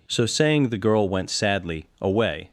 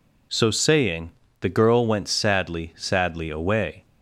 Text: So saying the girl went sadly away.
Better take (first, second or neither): first